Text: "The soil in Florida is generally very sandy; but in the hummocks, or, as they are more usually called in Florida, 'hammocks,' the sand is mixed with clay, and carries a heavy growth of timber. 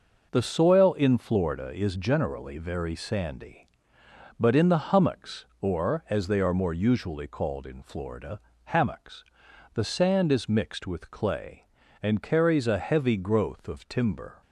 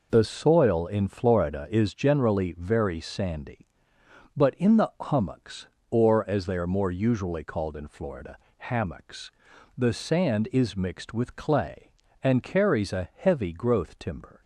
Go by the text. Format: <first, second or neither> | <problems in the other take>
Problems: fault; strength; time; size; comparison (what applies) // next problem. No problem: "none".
first | skips "of"; at 13.9 s